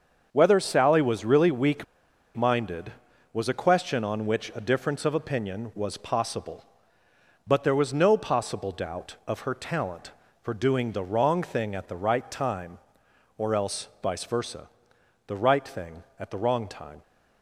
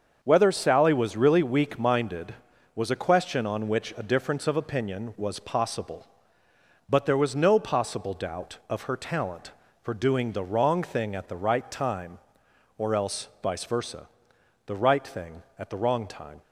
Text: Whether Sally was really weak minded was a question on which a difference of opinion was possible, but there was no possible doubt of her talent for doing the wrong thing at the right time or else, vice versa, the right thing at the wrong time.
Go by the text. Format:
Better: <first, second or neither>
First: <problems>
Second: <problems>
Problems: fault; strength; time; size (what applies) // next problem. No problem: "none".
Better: second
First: starts louder than the rest; until 1.3 s; 6.5 dB // pauses between "weak" and "minded"; noticeable; at 1.8 s; 0.52 s long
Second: starts louder than the rest; until 1.2 s; 6.5 dB